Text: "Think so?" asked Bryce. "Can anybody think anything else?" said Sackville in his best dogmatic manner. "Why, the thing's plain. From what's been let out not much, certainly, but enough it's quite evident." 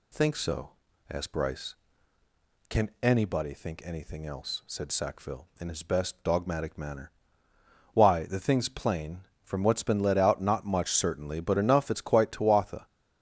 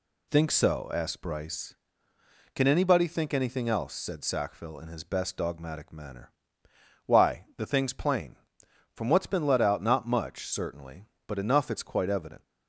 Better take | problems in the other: second | says "tuatha" for "evident"; at 12.3 s

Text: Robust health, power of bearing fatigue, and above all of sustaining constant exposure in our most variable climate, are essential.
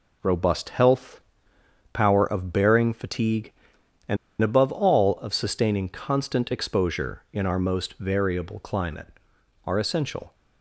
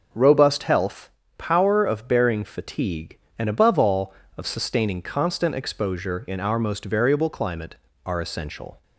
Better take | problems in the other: second | pauses between "and" and "above"; slight; at 4.1 s; 0.24 s long

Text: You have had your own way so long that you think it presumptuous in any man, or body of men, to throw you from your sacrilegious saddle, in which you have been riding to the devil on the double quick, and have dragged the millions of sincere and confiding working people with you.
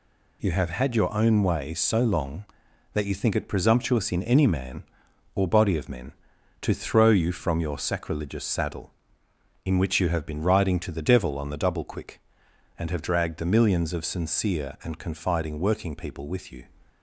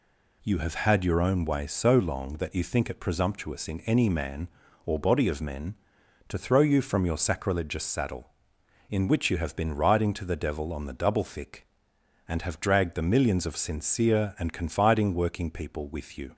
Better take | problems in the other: first | says "thick" for "quick"; at 11.2 s

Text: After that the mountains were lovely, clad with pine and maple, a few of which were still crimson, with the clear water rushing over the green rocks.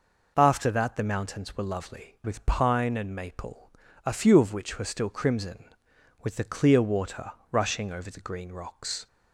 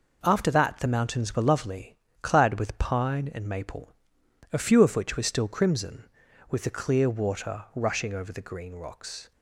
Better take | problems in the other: second | skips "clad"; at 2.1 s // pauses between "water" and "rushing"; slight; at 7.3 s; 0.18 s long

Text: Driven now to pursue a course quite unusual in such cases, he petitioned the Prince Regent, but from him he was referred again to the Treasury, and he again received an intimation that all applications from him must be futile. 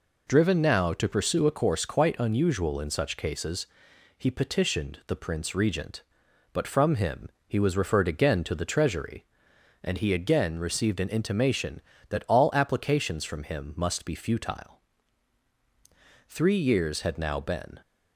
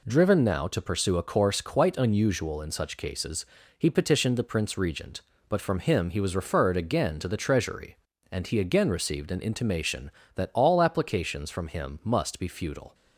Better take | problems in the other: second | pauses between "him" and "he"; slight; at 7.2 s; 0.18 s long // goes on to say "Three years had now been"; from 16.2 s on; 1.5 s long

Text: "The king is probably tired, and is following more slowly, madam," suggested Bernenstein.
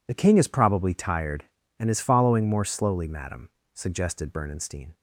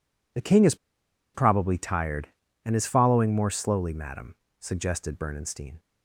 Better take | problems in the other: first | pauses between "is" and "probably"; noticeable; at 0.7 s; 0.59 s long

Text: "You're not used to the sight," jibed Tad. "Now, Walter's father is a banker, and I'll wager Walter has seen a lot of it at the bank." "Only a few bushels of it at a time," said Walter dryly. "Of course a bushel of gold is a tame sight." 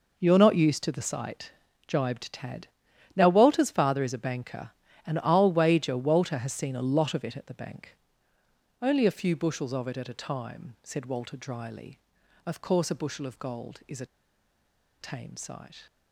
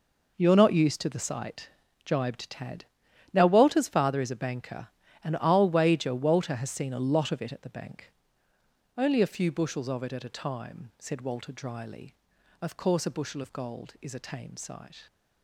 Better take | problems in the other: second | pauses between "a" and "tame"; noticeable; at 14.0 s; 0.94 s long

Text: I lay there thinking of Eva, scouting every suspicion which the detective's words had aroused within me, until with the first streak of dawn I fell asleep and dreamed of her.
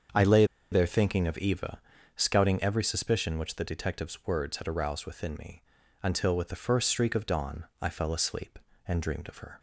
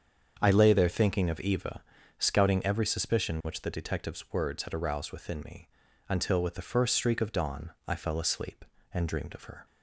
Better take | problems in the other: second | starts louder than the rest; strong; until 1.4 s; 7 dB; strong in the second // pauses between "lay" and "there"; slight; at 0.4 s; 0.27 s long // pauses between "dawn" and "I"; slight; at 7.6 s; 0.16 s long; slight in the second

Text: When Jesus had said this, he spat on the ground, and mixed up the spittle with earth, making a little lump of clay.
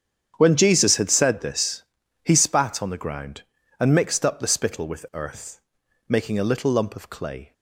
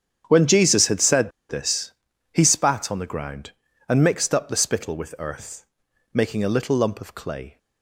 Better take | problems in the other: first | starts louder than the rest; strong; until 1.2 s; 8.5 dB; strong in the first // pauses between "said" and "this"; slight; at 1.3 s; 0.18 s long

